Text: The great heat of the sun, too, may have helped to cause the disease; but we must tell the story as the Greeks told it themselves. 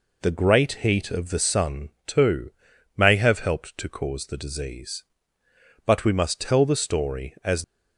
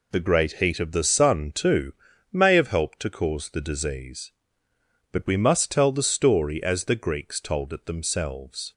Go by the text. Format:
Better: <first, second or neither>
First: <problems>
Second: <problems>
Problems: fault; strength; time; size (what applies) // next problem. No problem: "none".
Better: second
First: stops before "the Greeks told it themselves"; at 7.6 s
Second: none